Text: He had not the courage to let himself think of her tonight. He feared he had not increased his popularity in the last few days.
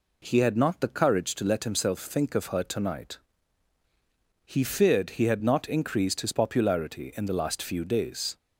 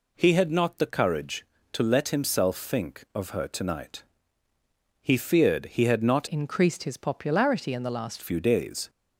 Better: first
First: none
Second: changes voice from "increased" to "last"; from 6.2 to 8.1 s; 1.9 s long

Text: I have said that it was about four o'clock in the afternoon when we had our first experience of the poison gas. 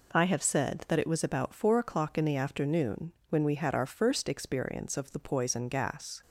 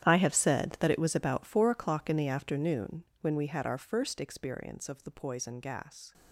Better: first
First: pauses between "afternoon" and "when"; slight; at 3.1 s; 0.18 s long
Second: gets quieter; strong; throughout; 17 dB // pauses between "afternoon" and "when"; slight; at 3.0 s; 0.18 s long

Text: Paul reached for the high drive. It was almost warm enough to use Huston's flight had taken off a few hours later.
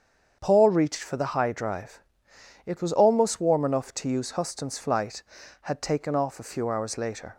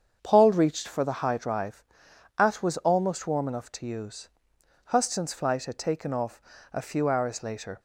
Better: first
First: starts louder than the rest; strong; until 1.4 s; 7.5 dB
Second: starts louder than the rest; strong; until 1.2 s; 7.5 dB // says "At" for "It"; at 2.3 s // pauses between "use" and "Huston's"; noticeable; at 4.2 s; 0.58 s long // pauses between "off" and "a"; slight; at 6.4 s; 0.32 s long

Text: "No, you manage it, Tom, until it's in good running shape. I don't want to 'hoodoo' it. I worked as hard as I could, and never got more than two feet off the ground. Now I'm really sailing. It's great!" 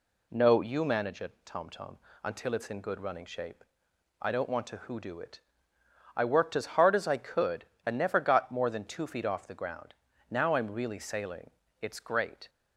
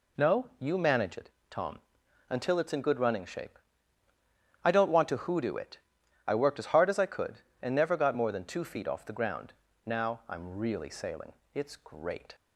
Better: second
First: says "Tom" twice; at 1.6 s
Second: none

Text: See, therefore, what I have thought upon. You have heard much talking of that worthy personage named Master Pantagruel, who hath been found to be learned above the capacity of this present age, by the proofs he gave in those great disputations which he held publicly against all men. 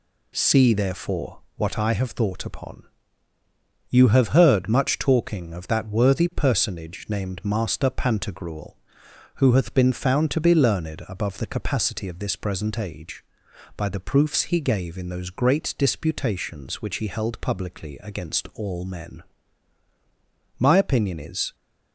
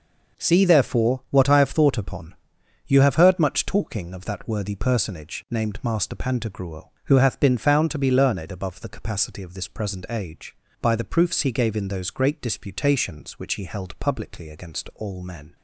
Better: second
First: goes on to say "My opinion is"; noticeable; from 20.5 s on; 0.96 s long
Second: none

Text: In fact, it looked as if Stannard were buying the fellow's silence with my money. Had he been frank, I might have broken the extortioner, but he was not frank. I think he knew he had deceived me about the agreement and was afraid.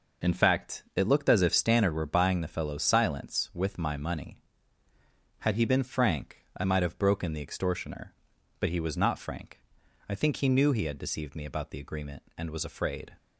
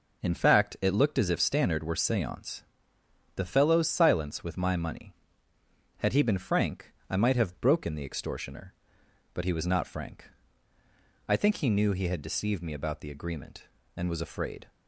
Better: first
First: none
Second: says "seance" for "buying"; at 1.9 s

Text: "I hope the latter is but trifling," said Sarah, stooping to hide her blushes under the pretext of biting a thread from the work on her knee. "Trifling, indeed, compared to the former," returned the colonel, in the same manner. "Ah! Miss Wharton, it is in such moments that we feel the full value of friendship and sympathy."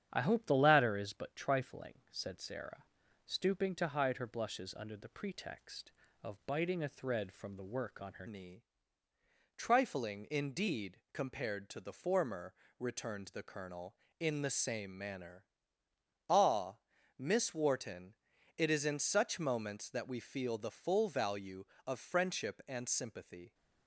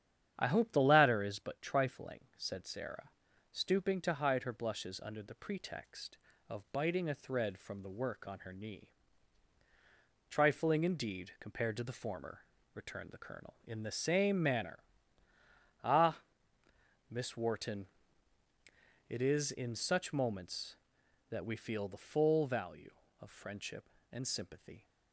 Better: second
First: starts louder than the rest; strong; until 1.1 s; 9 dB // changes voice at "knee"; from 8.2 s on; 15.3 s long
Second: starts louder than the rest; strong; until 1.3 s; 9.5 dB

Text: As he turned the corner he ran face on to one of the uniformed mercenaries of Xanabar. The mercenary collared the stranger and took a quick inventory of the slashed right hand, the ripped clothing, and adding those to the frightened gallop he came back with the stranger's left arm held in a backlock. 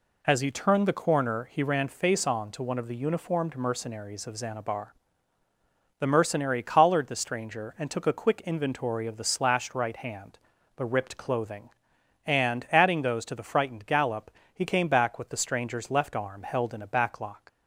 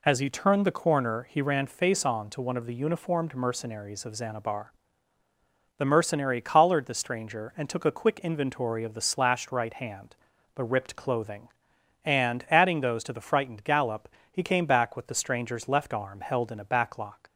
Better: neither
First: pauses between "gallop" and "he"; slight; at 14.3 s; 0.22 s long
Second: pauses between "gallop" and "he"; slight; at 14.0 s; 0.22 s long

